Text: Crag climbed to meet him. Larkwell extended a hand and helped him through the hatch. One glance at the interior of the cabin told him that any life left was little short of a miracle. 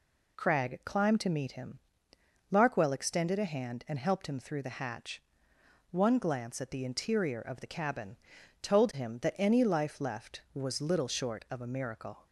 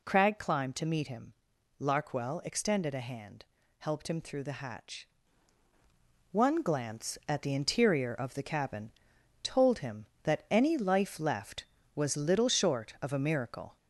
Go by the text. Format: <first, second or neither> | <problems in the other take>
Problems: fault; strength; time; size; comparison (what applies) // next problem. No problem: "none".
first | skips "and"; at 3.6 s // pauses between "cabin" and "told"; noticeable; at 8.9 s; 0.50 s long; also in the first